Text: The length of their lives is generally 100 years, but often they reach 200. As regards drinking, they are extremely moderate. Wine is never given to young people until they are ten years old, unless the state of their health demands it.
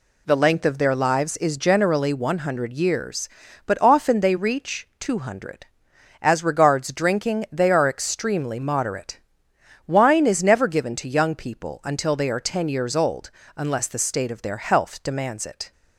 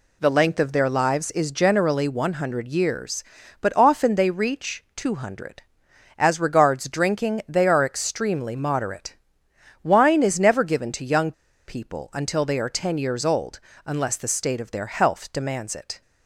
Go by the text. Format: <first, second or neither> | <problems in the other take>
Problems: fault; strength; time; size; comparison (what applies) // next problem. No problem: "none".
first | pauses between "young" and "people"; slight; at 11.3 s; 0.35 s long